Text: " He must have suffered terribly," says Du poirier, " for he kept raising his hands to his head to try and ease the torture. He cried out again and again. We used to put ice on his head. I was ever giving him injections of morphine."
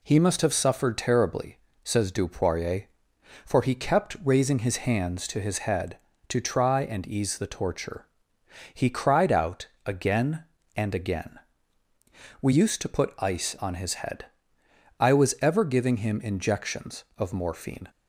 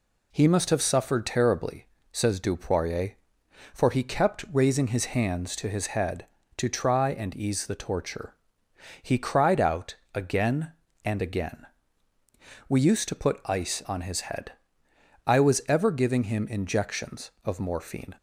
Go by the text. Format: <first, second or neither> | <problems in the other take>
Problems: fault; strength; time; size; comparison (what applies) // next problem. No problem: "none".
neither | pauses between "out" and "again"; slight; the same in both